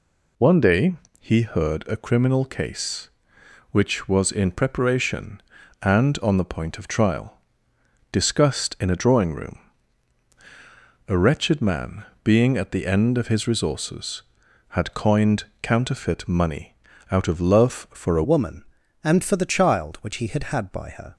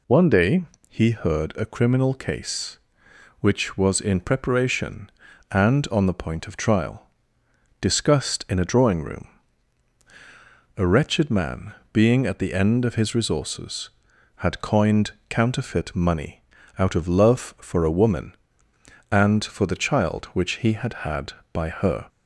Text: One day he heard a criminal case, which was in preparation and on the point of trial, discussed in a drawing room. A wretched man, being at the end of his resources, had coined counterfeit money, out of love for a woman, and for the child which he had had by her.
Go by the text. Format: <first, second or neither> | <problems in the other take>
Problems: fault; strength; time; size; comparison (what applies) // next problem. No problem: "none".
second | pauses between "day" and "he"; slight; at 0.9 s; 0.26 s long; slight in the second // pauses between "coined" and "counterfeit"; slight; at 15.4 s; 0.16 s long; slight in the second // changes voice at "woman"; from 18.2 s on; 2.9 s long